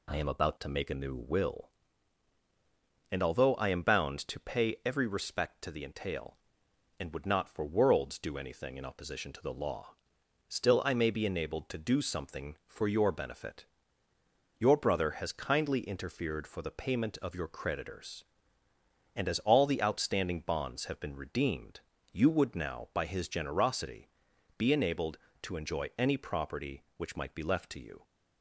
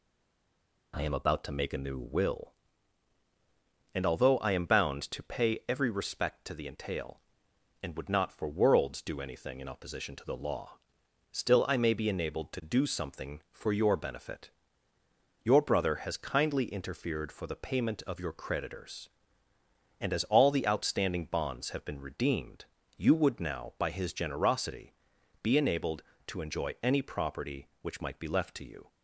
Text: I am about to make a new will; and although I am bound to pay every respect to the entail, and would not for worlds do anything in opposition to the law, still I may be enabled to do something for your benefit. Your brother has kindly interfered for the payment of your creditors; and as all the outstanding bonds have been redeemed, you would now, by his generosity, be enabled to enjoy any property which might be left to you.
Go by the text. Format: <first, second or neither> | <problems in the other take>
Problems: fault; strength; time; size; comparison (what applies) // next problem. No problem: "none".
first | stays silent before the first word; slight; until 0.9 s; 0.9 s long